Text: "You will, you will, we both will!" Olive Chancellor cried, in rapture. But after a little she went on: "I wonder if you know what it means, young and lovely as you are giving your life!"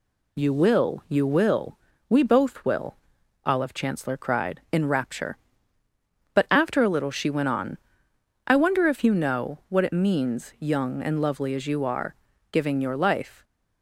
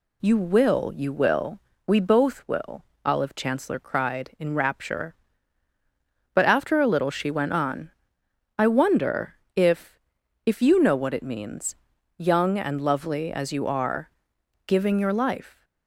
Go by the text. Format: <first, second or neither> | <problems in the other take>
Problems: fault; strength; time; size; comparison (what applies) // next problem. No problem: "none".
first | pauses between "wonder" and "if"; slight; at 9.3 s; 0.20 s long // says "if" twice; at 10.4 s // pauses between "are" and "giving"; noticeable; at 14.1 s; 0.56 s long; slight in the first